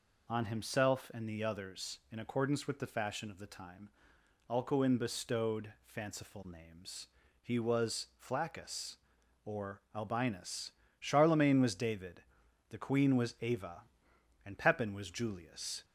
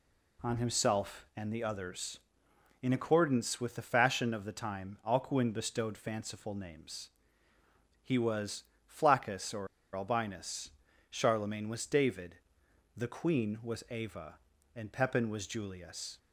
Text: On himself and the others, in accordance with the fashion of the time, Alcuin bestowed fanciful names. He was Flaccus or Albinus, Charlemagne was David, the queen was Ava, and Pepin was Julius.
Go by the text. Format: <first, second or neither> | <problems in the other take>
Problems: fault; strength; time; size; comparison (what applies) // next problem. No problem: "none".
first | pauses between "was" and "Flaccus"; slight; at 8.6 s; 0.24 s long // pauses between "or" and "Albinus"; slight; at 9.6 s; 0.28 s long